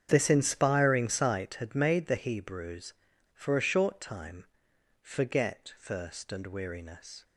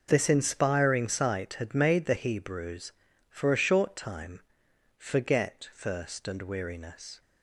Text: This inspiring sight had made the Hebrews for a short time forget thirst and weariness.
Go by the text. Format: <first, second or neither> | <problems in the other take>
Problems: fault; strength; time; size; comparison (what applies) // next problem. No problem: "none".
second | starts louder than the rest; strong; until 1.6 s; 8 dB // pauses between "time" and "forget"; noticeable; at 4.4 s; 0.56 s long; noticeable in the second